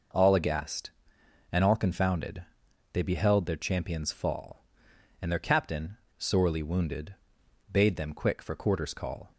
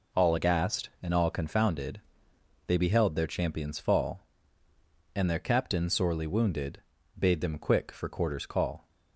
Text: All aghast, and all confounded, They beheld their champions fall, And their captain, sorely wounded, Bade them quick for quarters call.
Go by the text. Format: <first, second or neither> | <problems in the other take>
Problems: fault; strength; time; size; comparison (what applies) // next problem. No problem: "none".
neither | none